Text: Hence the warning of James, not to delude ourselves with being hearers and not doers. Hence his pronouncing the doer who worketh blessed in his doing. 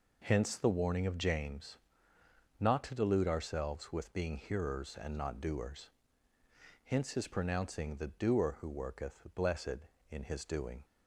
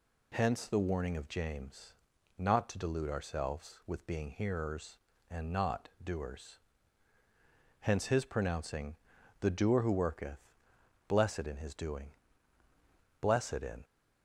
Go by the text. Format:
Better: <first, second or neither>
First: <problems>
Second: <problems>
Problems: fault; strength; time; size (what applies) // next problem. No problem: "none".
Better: first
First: none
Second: pauses between "pronouncing" and "the"; noticeable; at 8.9 s; 0.46 s long // pauses between "worketh" and "blessed"; noticeable; at 10.3 s; 0.68 s long // goes on to say "Blessed in"; noticeable; from 13.2 s on; 0.62 s long